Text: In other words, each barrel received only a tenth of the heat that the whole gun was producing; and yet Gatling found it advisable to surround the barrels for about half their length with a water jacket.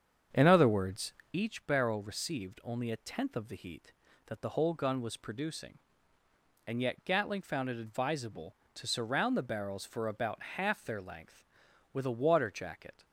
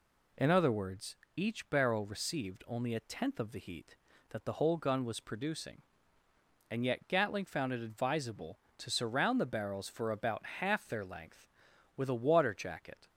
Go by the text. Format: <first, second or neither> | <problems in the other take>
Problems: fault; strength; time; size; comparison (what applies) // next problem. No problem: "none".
second | starts louder than the rest; strong; until 1.4 s; 7.5 dB